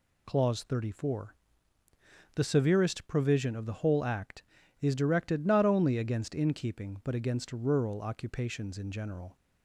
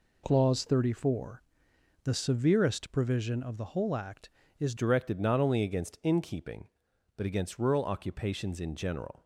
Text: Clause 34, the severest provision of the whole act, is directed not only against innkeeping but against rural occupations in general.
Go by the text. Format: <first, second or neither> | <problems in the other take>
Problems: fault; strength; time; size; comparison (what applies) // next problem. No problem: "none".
first | changes voice at "directed"; from 4.7 s on; 4.5 s long